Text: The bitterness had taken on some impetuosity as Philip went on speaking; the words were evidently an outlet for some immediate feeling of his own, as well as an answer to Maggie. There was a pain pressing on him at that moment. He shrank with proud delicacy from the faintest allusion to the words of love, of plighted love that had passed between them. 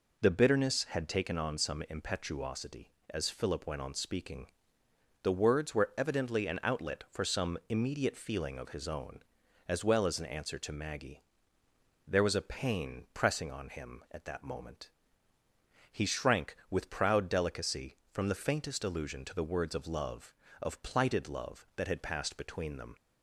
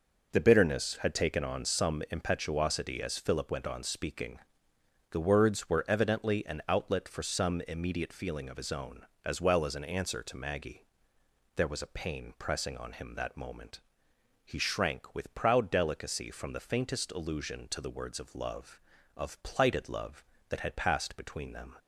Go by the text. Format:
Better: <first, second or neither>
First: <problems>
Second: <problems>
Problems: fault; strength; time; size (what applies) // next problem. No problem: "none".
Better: first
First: none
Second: skips "at"; at 13.1 s